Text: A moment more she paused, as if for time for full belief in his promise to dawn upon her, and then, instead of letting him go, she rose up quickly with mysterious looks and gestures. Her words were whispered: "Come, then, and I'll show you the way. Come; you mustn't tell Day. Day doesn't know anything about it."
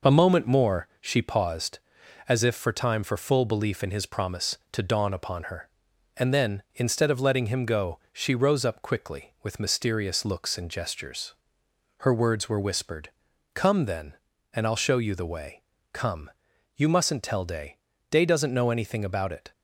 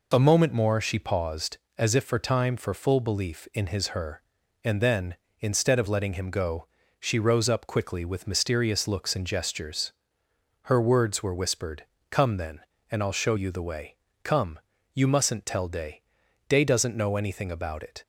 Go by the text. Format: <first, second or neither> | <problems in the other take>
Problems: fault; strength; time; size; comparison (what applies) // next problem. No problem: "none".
first | skips "promise to dawn upon"; at 3.8 s